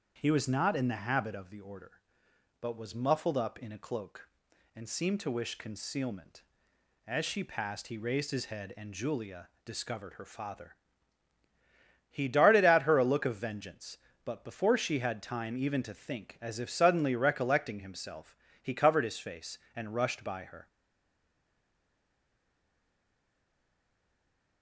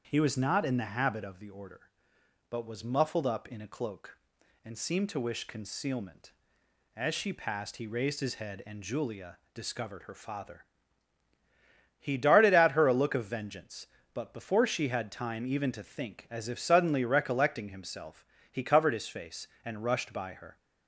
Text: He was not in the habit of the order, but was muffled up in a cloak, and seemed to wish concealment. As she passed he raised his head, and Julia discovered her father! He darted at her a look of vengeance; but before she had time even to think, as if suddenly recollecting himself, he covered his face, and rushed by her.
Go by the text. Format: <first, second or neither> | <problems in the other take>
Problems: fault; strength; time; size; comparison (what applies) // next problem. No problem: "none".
second | starts louder than the rest; strong; until 1.2 s; 7.5 dB; strong in the second // pauses between "Julia" and "discovered"; slight; at 9.4 s; 0.16 s long; slight in the second // stays silent after the last word; strong; from 20.6 s on; 4.0 s long